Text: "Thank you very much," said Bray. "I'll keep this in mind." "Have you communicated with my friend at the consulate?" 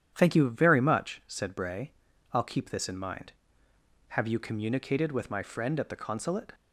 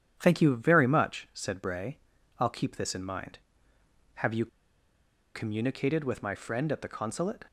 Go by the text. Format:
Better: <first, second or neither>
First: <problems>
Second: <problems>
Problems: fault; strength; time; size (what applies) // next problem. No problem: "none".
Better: first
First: starts louder than the rest; strong; until 1.1 s; 9.5 dB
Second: starts louder than the rest; strong; until 1.1 s; 9.5 dB // pauses between "you" and "communicated"; noticeable; at 4.4 s; 0.87 s long